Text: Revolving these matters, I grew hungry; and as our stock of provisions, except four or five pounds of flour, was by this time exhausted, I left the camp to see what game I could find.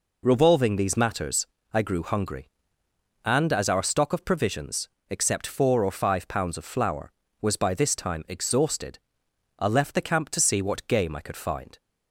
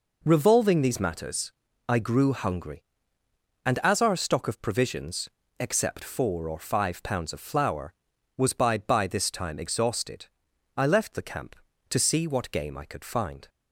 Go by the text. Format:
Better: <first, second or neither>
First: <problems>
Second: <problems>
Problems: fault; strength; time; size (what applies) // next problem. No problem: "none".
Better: first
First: none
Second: says "by" twice; at 8.7 s